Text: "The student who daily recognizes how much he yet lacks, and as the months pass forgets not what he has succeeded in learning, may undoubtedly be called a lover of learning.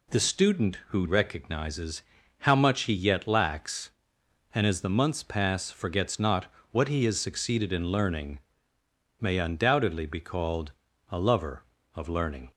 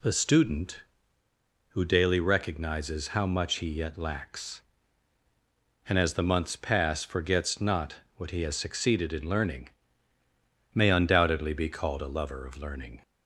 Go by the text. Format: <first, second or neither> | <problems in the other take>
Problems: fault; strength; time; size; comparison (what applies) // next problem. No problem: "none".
second | skips "daily"; at 1.0 s // pauses between "recognizes" and "how"; at 2.0 s; 0.38 s long // pauses between "not" and "what"; slight; at 6.5 s; 0.20 s long; slight in the second // pauses between "called" and "a"; at 10.7 s; 0.40 s long